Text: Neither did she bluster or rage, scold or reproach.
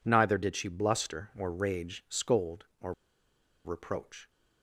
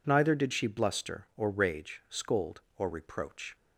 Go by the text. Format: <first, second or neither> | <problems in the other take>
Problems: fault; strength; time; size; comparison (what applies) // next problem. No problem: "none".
second | pauses between "or" and "reproach"; noticeable; at 2.9 s; 0.73 s long